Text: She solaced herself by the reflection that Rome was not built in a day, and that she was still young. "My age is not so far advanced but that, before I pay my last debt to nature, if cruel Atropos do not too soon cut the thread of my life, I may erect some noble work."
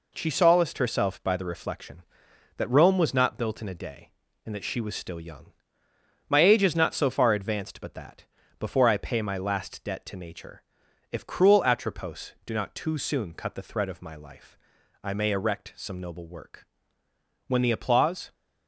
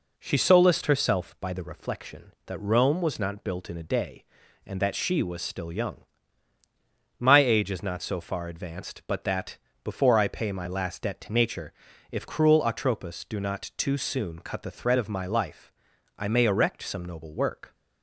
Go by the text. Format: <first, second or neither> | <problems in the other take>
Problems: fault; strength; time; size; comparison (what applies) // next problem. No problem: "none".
second | goes on to say "When the applause"; noticeable; from 17.4 s on; 0.86 s long